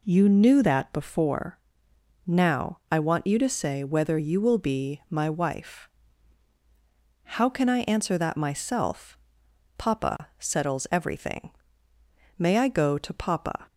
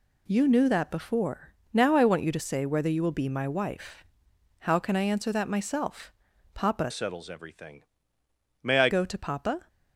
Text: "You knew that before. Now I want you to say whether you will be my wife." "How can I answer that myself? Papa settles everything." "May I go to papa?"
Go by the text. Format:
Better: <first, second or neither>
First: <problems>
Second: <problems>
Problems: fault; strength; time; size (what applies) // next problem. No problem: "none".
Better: first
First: none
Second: changes voice from "settles" to "I"; from 6.9 to 8.8 s; 1.9 s long